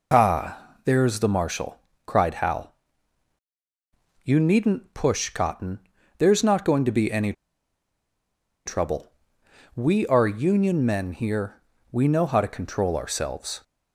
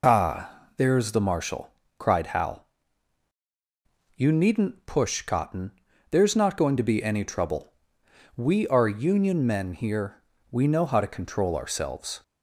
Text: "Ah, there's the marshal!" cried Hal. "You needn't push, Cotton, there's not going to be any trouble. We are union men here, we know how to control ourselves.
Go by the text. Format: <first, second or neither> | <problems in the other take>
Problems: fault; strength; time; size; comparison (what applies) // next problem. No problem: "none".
second | pauses between "any" and "trouble"; strong; at 7.3 s; 1.3 s long